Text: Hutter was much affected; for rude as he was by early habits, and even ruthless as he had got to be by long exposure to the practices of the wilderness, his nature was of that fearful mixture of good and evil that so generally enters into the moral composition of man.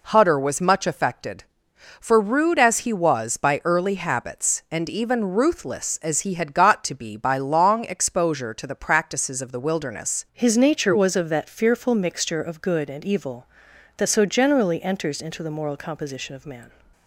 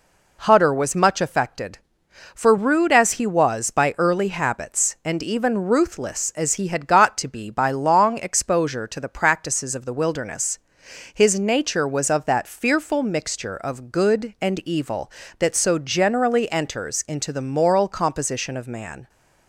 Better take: second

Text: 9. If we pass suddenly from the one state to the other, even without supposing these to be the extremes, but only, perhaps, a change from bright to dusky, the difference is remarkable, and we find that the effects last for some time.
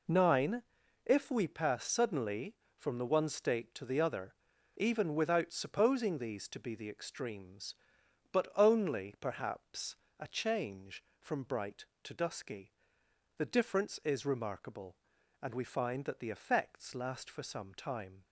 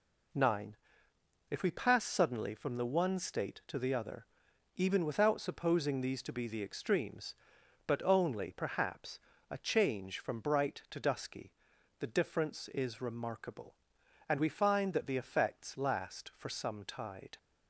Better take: first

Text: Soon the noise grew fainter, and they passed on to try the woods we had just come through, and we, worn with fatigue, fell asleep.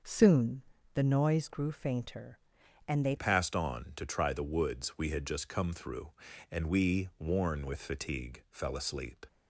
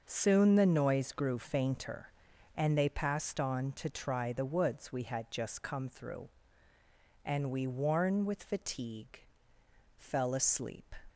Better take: second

